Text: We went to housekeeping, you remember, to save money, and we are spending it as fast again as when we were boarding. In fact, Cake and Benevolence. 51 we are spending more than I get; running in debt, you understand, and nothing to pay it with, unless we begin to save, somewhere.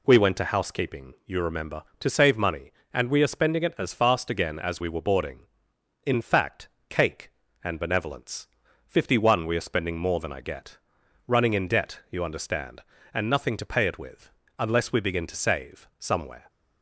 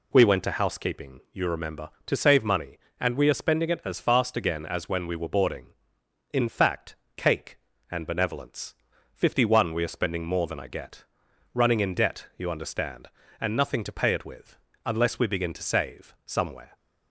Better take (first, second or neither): second